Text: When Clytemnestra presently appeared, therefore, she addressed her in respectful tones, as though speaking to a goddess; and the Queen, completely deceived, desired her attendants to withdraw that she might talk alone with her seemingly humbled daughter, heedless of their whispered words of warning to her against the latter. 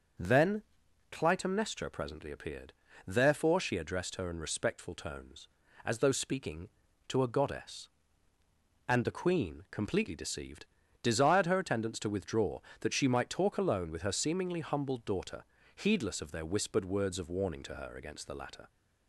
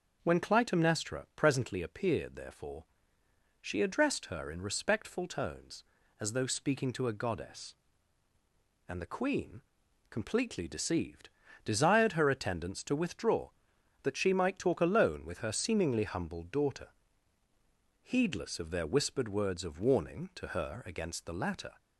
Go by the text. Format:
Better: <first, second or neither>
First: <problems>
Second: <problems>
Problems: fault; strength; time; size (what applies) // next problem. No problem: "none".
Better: second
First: starts louder than the rest; until 1.6 s; 6 dB // says "Then" for "When"; at 0.1 s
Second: starts louder than the rest; until 1.2 s; 6.5 dB